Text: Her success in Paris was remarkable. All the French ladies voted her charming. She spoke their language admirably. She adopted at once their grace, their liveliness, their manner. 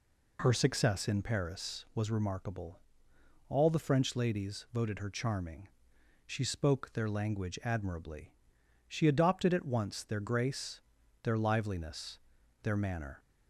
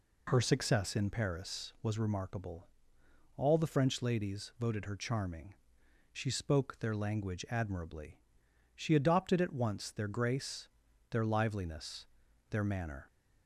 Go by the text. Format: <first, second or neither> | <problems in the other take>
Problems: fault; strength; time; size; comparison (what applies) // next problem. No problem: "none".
neither | none